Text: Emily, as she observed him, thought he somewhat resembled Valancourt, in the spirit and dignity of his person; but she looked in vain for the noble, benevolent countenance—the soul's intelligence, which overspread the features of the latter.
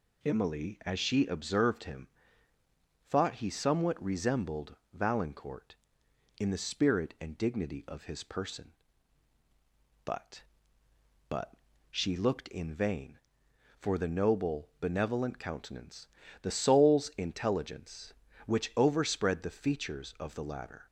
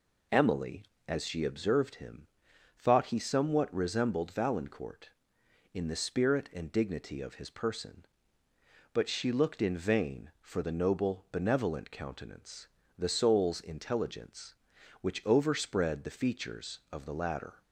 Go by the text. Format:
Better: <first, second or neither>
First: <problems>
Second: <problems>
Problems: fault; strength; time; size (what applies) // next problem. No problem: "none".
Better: second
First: pauses between "resembled" and "Valancourt"; slight; at 4.7 s; 0.18 s long // says "but" twice; at 11.2 s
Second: none